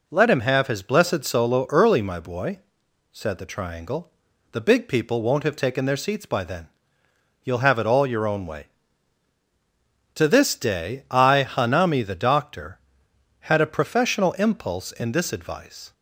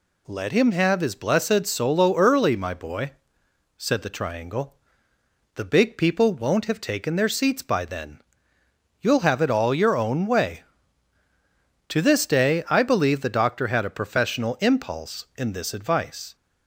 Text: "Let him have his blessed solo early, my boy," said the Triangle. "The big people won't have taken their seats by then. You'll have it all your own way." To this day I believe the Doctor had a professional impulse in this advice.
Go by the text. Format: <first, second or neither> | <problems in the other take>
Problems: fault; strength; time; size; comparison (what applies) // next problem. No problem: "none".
second | says "hanami" for "believe"; at 11.4 s